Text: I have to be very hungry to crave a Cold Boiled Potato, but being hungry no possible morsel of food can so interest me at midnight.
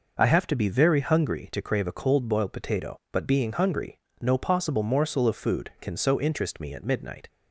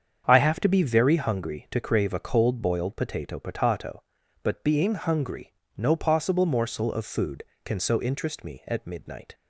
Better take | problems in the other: first | starts louder than the rest; strong; until 1.2 s; 7.5 dB // says "Potato" twice; at 3.3 s // pauses between "hungry" and "no"; slight; at 5.5 s; 0.24 s long; slight in the first

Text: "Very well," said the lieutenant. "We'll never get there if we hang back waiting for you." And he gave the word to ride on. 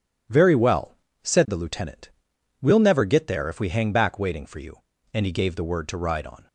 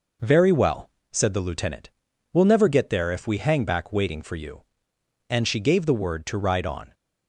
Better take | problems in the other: first | says "she" for "he"; at 5.4 s

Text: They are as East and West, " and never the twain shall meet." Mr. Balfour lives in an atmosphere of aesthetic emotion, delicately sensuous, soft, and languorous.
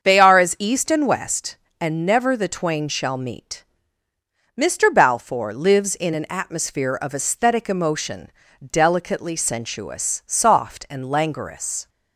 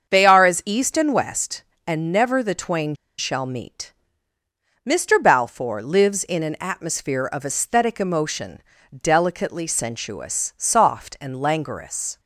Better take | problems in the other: first | starts louder than the rest; until 1.1 s; 7 dB; also in the first // pauses between "twain" and "shall"; slight; at 2.9 s; 0.22 s long

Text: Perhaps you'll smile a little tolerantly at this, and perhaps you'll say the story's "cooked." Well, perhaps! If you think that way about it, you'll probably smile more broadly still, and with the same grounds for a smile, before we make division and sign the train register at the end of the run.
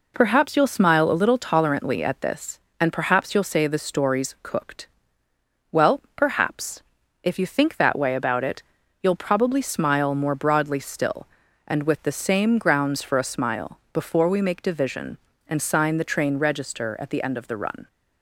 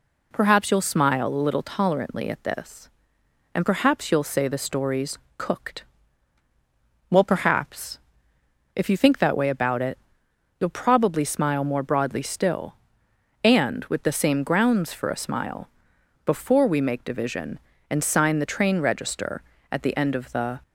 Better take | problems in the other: first | pauses between "story's" and "cooked"; slight; at 5.1 s; 0.18 s long // stops before "run"; at 20.6 s

